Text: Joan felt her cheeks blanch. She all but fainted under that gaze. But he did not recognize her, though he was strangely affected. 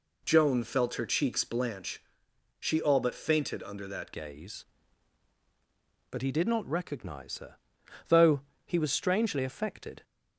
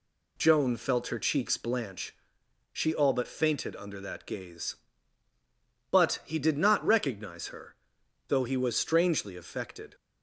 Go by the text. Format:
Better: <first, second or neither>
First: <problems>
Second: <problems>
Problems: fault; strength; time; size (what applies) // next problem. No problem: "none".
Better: second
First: changes voice at "gaze"; from 4.1 s on; 5.9 s long // pauses between "though" and "he"; slight; at 8.4 s; 0.24 s long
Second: none